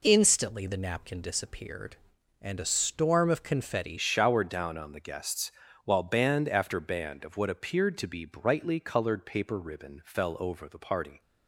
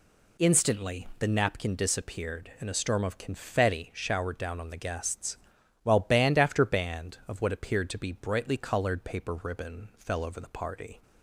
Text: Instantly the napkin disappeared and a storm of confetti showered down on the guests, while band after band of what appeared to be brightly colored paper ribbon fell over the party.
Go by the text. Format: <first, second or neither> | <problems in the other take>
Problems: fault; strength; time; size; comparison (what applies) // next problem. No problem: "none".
second | changes voice at "showered"; from 3.9 s on; 7.3 s long